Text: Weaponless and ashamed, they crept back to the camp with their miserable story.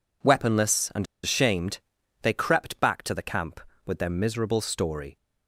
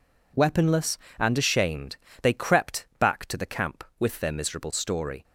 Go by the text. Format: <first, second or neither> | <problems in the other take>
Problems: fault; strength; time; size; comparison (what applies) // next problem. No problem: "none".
second | pauses between "and" and "ashamed"; slight; at 1.0 s; 0.18 s long